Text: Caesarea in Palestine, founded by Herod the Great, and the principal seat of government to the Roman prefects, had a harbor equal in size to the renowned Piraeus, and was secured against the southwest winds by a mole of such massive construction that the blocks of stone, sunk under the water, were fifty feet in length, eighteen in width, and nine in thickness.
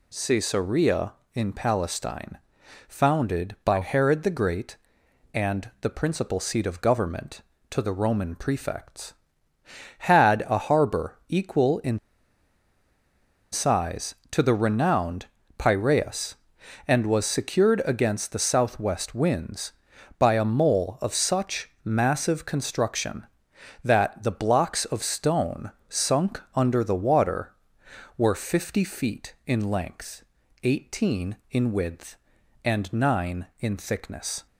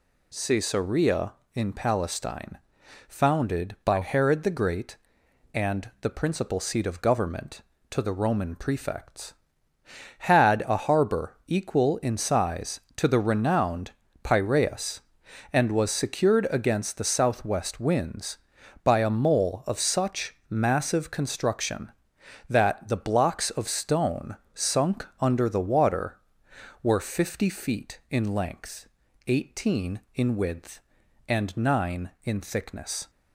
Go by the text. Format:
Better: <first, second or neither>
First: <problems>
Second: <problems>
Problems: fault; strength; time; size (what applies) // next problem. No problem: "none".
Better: second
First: pauses between "in" and "size"; strong; at 11.9 s; 1.5 s long // pauses between "renowned" and "Piraeus"; slight; at 15.2 s; 0.32 s long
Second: pauses between "renowned" and "Piraeus"; slight; at 13.9 s; 0.32 s long